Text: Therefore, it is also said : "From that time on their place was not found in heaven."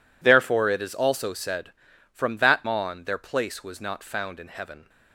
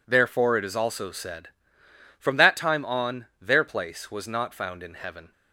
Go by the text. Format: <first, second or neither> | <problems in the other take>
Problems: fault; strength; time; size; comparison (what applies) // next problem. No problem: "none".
second | skips "time"; at 2.6 s